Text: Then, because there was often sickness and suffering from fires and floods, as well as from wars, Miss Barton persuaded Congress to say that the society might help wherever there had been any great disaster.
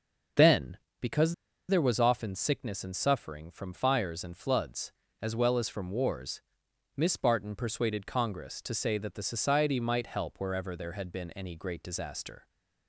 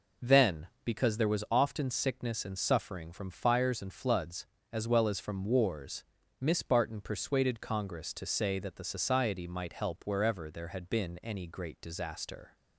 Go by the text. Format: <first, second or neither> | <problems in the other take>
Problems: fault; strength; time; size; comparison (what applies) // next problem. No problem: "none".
second | pauses between "because" and "there"; slight; at 1.3 s; 0.35 s long